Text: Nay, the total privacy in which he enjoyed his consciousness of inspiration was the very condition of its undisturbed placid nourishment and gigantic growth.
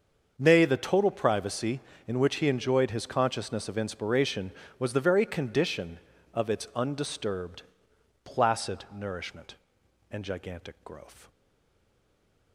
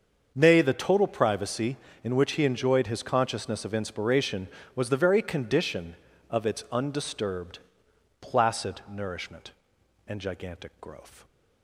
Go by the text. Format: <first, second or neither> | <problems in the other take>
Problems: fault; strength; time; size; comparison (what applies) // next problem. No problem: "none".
second | starts louder than the rest; until 1.3 s; 6.5 dB; also in the second // pauses between "undisturbed" and "placid"; noticeable; at 7.6 s; 0.62 s long; noticeable in the second // stays silent after the last word; noticeable; from 11.2 s on; 1.3 s long